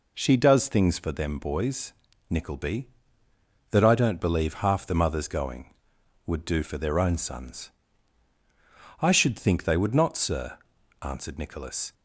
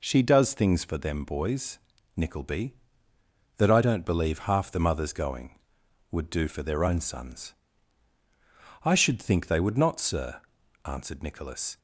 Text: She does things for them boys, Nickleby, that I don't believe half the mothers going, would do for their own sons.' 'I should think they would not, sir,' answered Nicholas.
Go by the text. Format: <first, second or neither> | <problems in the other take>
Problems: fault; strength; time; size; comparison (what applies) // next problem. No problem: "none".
neither | none